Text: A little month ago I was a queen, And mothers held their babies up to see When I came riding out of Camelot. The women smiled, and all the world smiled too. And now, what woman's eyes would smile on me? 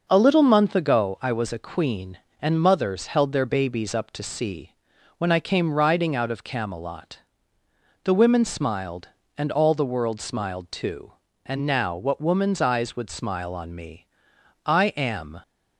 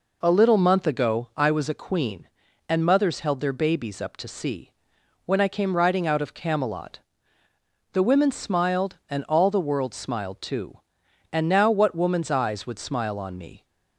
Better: second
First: pauses between "see" and "When"; noticeable; at 4.7 s; 0.46 s long // goes on to say "I am"; noticeable; from 14.6 s on; 0.76 s long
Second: pauses between "see" and "When"; noticeable; at 4.6 s; 0.56 s long

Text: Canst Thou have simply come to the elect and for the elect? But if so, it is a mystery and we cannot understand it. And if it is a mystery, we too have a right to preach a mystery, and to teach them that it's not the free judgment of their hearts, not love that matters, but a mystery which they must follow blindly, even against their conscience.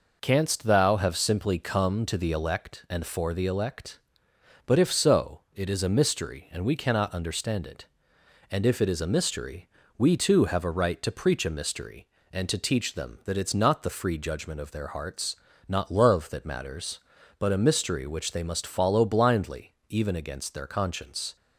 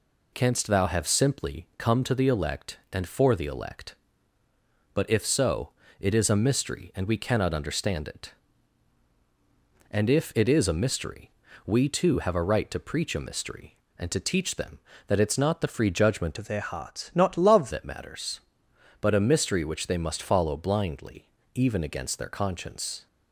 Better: first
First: none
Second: changes voice from "of" to "love"; from 16.3 to 17.7 s; 1.4 s long

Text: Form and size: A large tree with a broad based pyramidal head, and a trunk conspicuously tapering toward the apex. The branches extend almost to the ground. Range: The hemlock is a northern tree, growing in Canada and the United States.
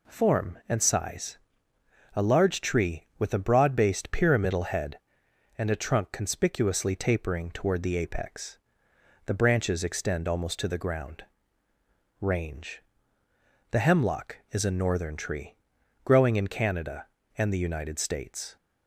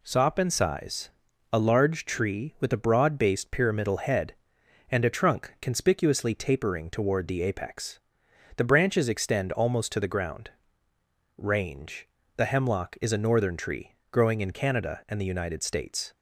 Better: first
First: none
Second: says "Sop" for "Form"; at 0.0 s

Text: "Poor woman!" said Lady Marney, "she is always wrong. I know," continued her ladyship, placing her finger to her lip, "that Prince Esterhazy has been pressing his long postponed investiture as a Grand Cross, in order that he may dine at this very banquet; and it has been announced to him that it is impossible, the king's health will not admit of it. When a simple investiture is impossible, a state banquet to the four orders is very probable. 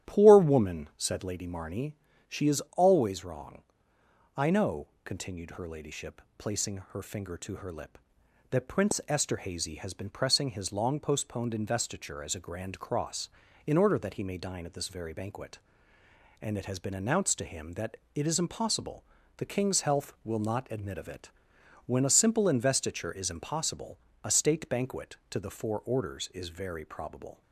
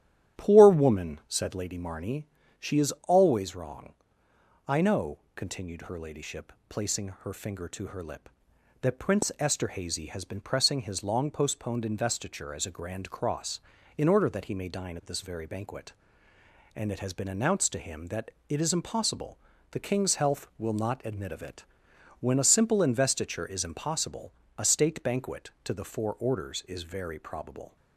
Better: neither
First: starts louder than the rest; strong; until 1.1 s; 10 dB // pauses between "is" and "always"; slight; at 2.6 s; 0.16 s long // pauses between "that" and "it"; slight; at 17.9 s; 0.20 s long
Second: starts louder than the rest; strong; until 1.4 s; 10 dB // pauses between "is" and "always"; slight; at 2.9 s; 0.16 s long // pauses between "that" and "it"; slight; at 18.2 s; 0.20 s long

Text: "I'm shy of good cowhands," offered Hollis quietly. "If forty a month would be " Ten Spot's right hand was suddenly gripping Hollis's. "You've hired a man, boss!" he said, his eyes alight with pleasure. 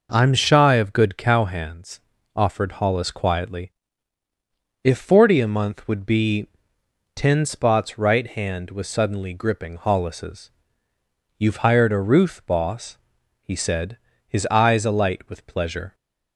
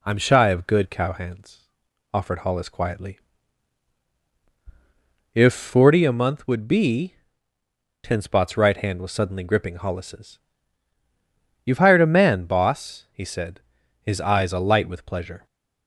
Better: second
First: says "ruth" for "man"; at 11.9 s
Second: none

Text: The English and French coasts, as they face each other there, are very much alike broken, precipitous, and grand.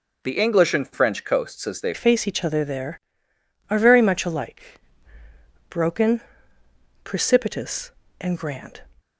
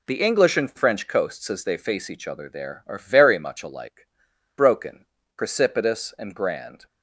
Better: second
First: changes voice at "face"; from 1.9 s on; 6.9 s long // pauses between "alike" and "broken"; noticeable; at 4.7 s; 0.92 s long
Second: pauses between "alike" and "broken"; noticeable; at 4.0 s; 0.50 s long

